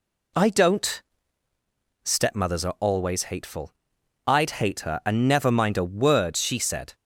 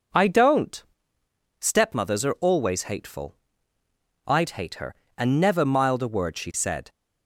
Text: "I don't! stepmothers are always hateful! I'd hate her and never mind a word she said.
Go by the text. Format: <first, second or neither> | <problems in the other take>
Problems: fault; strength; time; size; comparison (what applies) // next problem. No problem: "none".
first | says "mild" for "mind"; at 5.6 s